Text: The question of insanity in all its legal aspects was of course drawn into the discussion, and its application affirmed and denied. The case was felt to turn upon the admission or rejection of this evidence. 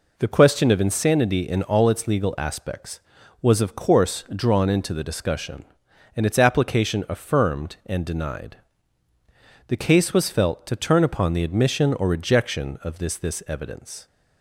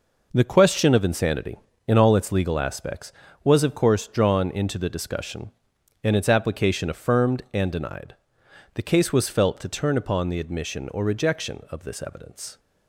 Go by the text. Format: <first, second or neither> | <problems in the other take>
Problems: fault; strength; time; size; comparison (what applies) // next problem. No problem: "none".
second | says "this" twice; at 13.1 s